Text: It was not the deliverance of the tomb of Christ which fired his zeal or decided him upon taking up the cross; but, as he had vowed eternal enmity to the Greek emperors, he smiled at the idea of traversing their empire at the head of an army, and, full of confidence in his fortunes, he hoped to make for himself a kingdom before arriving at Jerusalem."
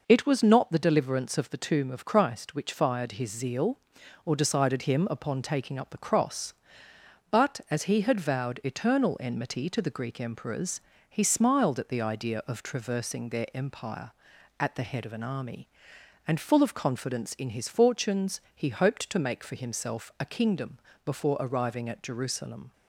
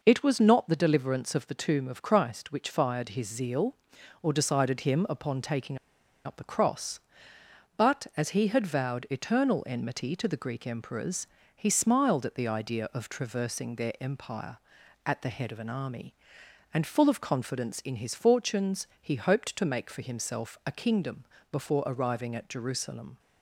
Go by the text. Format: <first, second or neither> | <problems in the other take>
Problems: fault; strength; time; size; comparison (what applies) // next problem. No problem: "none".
first | pauses between "taking" and "up"; noticeable; at 5.7 s; 0.47 s long // pauses between "kingdom" and "before"; slight; at 21.2 s; 0.26 s long; slight in the first